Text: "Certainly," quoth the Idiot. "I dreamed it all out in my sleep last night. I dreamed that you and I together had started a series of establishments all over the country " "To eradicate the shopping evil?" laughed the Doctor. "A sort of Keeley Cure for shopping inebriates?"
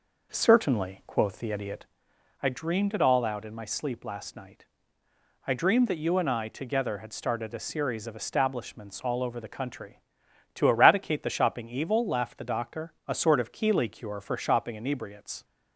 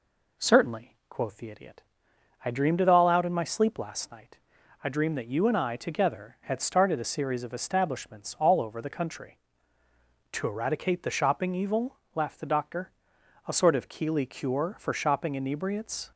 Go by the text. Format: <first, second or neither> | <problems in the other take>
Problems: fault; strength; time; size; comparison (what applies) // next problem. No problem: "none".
second | starts louder than the rest; noticeable; until 2.0 s; 5.5 dB